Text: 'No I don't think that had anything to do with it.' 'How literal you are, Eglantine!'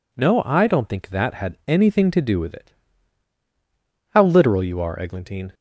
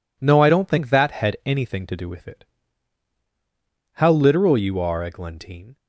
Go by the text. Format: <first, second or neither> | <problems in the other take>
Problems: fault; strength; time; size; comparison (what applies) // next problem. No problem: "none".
neither | none